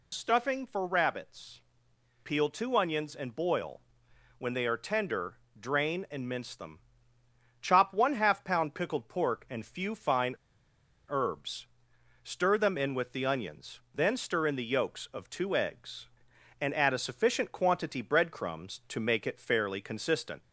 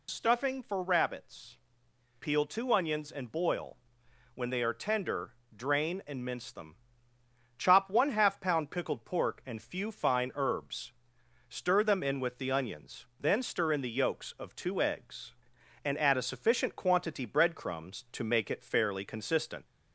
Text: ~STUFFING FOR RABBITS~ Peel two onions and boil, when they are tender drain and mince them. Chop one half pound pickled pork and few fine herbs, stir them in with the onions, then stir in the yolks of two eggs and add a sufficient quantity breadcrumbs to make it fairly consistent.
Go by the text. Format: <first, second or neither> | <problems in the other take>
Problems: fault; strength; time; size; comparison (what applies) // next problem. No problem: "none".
second | pauses between "tender" and "drain"; slight; at 5.3 s; 0.20 s long; slight in the second // pauses between "fine" and "herbs"; noticeable; at 10.3 s; 0.72 s long